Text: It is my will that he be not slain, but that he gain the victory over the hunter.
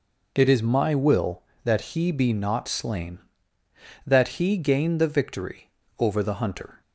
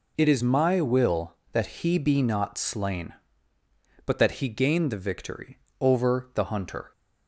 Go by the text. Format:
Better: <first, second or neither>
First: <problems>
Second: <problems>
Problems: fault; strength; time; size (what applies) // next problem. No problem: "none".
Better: second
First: skips "but"; at 3.6 s // pauses between "victory" and "over"; slight; at 5.6 s; 0.28 s long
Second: pauses between "victory" and "over"; slight; at 5.5 s; 0.22 s long